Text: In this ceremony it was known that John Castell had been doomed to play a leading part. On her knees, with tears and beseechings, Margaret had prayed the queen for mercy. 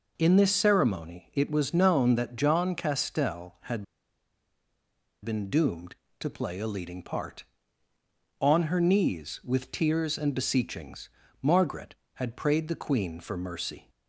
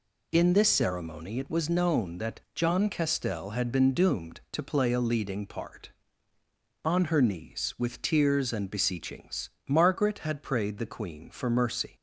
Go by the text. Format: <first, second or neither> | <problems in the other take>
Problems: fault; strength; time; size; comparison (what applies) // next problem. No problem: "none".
second | pauses between "had" and "been"; strong; at 3.8 s; 1.4 s long